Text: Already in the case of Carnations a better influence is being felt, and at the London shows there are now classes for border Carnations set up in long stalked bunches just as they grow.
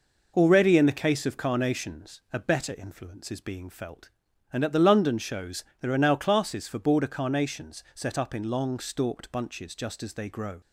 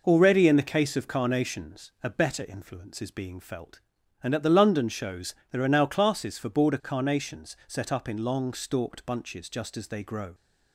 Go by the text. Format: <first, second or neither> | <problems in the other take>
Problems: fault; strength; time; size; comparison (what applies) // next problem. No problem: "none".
neither | pauses between "shows" and "there"; slight; the same in both